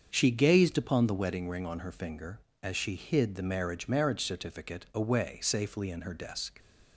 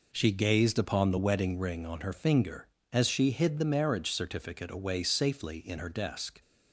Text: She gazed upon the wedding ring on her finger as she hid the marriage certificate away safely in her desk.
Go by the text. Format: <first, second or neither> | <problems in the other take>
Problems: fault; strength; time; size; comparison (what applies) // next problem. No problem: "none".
second | starts louder than the rest; until 1.1 s; 7 dB // says "marriage" twice; at 3.8 s